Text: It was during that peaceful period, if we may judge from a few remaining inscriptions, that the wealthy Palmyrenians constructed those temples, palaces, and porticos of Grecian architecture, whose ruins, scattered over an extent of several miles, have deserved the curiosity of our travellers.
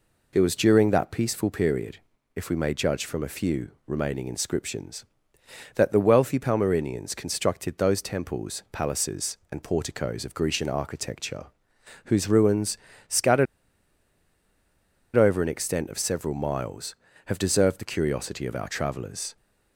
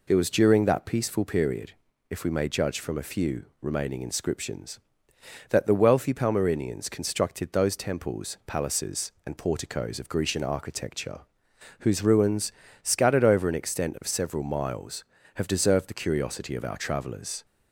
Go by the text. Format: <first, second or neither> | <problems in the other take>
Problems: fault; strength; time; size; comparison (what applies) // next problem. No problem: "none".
second | pauses between "few" and "remaining"; slight; at 3.6 s; 0.16 s long; slight in the second // pauses between "scattered" and "over"; strong; at 13.4 s; 1.7 s long